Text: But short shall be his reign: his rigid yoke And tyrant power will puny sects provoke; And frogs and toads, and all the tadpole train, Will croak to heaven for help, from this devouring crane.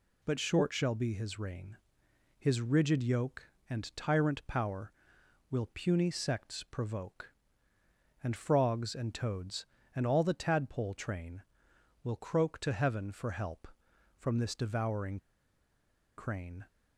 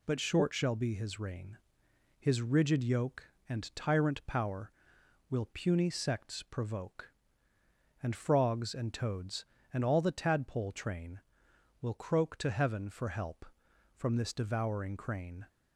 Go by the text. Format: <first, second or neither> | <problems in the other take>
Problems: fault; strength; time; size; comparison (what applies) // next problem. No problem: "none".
second | pauses between "devouring" and "crane"; at 15.1 s; 0.99 s long